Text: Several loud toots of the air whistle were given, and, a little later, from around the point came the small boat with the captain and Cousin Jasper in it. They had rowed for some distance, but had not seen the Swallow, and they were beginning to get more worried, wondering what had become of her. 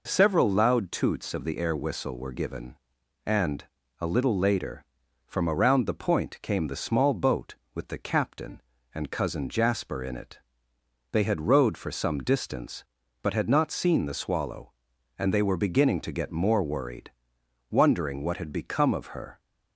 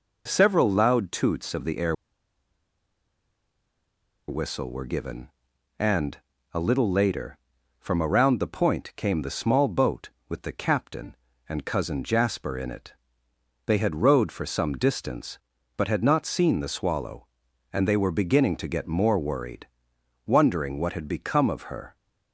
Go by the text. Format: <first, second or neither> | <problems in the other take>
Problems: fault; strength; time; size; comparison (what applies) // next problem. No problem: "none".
first | pauses between "air" and "whistle"; strong; at 1.9 s; 2.3 s long